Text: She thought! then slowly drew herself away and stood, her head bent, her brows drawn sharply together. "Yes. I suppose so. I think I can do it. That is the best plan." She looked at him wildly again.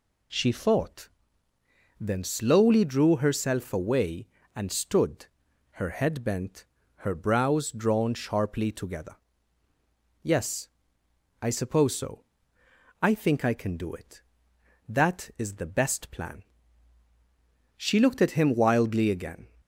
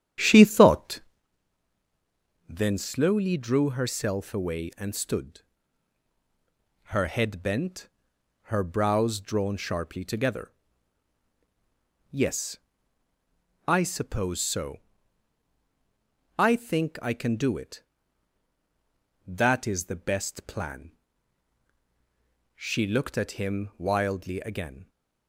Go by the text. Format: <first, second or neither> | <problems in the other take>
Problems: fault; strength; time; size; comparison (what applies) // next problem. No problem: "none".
first | starts louder than the rest; strong; until 1.3 s; 9.5 dB